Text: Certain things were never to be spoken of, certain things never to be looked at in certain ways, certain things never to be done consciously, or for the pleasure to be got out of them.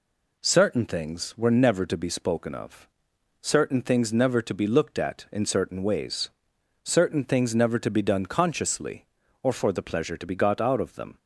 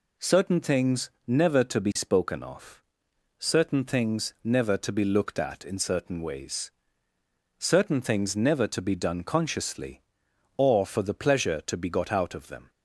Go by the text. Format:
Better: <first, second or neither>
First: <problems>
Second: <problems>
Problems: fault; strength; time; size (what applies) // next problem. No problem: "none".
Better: first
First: none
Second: skips "were"; at 1.1 s